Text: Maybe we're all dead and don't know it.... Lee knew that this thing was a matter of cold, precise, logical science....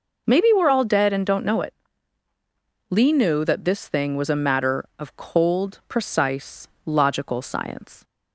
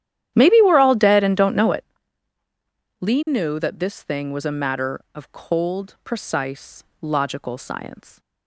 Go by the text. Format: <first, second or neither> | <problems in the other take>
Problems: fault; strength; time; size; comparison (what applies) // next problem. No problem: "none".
first | starts louder than the rest; strong; until 2.1 s; 11 dB